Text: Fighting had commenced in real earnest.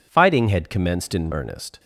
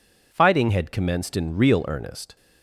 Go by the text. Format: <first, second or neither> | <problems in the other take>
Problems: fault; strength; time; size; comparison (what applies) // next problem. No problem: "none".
second | skips "real"; at 1.3 s